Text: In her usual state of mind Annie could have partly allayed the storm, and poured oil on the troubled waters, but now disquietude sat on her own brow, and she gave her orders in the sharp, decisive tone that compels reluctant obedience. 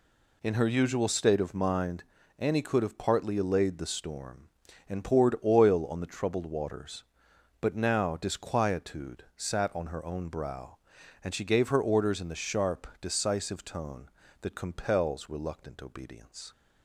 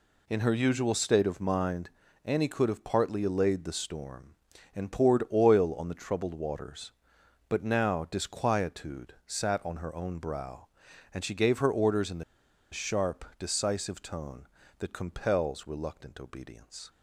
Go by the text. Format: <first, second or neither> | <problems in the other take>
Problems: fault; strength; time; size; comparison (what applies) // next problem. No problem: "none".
first | pauses between "mind" and "Annie"; slight; at 1.8 s; 0.34 s long; slight in the first // pauses between "the" and "sharp"; noticeable; at 12.2 s; 0.49 s long